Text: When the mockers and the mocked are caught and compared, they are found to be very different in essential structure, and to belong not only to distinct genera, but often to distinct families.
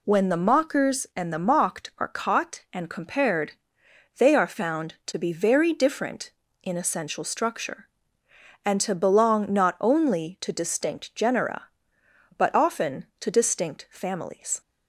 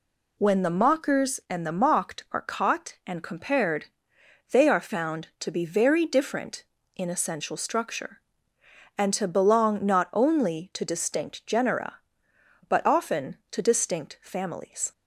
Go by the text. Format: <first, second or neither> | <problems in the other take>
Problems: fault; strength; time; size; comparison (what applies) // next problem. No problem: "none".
neither | none